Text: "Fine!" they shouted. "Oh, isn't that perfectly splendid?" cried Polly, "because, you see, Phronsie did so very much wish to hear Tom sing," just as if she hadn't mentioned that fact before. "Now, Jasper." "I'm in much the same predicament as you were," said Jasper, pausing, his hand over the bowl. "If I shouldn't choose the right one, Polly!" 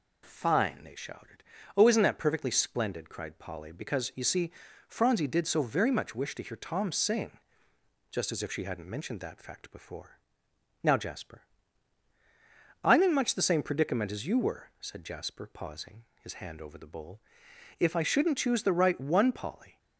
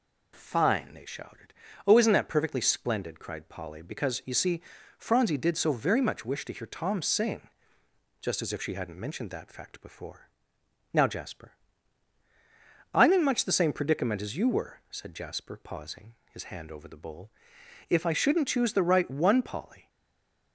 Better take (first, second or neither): first